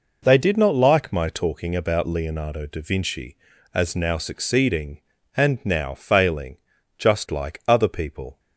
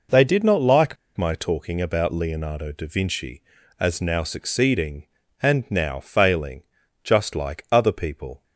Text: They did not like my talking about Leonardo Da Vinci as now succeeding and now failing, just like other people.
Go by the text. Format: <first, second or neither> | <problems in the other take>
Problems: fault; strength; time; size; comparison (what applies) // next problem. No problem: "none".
first | pauses between "like" and "my"; slight; at 0.9 s; 0.21 s long